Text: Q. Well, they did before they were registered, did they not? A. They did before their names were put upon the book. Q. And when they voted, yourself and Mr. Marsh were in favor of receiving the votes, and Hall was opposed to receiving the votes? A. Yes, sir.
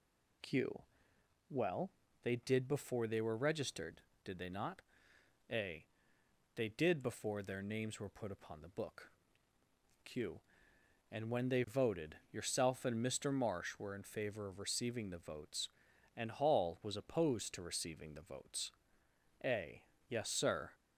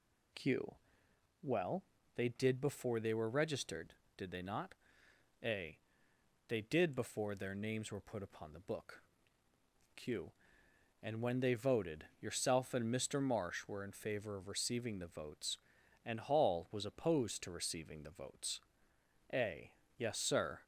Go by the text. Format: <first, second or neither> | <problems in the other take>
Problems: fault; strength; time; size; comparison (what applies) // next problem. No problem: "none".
neither | none